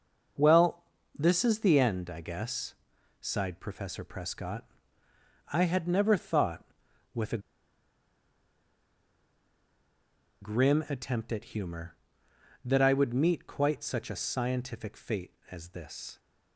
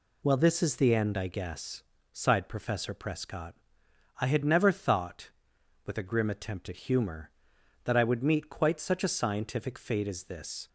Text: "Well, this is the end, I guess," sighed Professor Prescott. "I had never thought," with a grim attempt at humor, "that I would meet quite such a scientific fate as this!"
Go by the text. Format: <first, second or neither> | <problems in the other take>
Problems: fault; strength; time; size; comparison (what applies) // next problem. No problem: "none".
second | pauses between "a" and "grim"; strong; at 7.3 s; 3.0 s long